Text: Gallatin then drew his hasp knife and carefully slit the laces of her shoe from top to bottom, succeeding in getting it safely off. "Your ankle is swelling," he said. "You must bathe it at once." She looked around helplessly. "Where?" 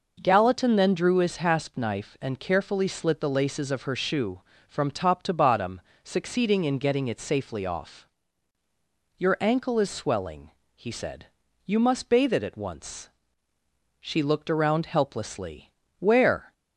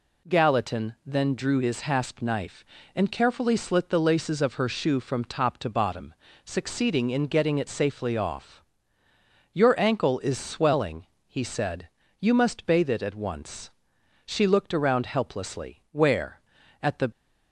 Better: first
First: none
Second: goes on to say "At the"; slight; from 16.8 s on; 0.20 s long

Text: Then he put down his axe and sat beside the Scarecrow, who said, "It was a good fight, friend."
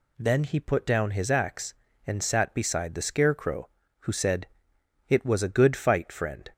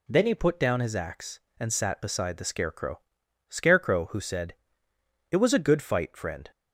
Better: first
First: none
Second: says "Scarecrow" twice; at 3.4 s

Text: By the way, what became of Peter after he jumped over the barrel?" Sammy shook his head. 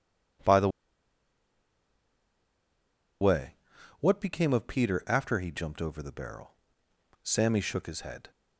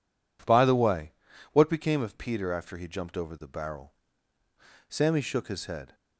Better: second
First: pauses between "the" and "way"; strong; at 0.6 s; 2.5 s long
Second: none

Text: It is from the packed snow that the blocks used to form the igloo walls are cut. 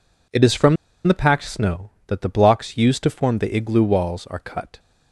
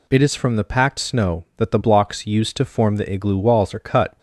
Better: second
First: pauses between "from" and "the"; slight; at 0.7 s; 0.31 s long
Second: none

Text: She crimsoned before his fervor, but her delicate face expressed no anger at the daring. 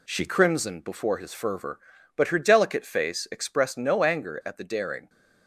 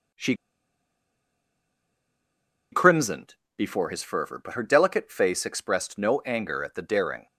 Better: first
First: none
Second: pauses between "She" and "crimsoned"; strong; at 0.3 s; 2.3 s long // pauses between "crimsoned" and "before"; slight; at 3.3 s; 0.24 s long

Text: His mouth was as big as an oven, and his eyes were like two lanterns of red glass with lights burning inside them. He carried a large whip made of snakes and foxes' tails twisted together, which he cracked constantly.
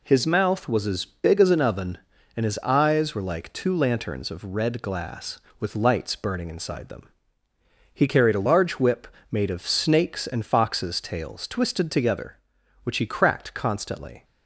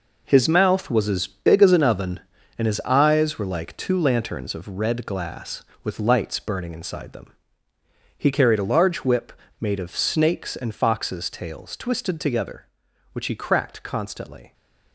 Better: first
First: pauses between "whip" and "made"; slight; at 9.0 s; 0.22 s long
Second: gets quieter; strong; throughout; 8 dB // pauses between "whip" and "made"; slight; at 9.3 s; 0.26 s long

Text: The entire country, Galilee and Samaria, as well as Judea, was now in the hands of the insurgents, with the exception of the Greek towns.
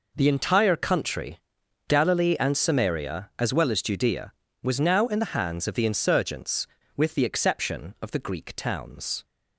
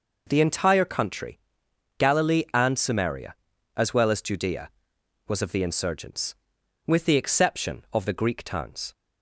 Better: first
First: none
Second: skips "now in the hands"; at 5.4 s

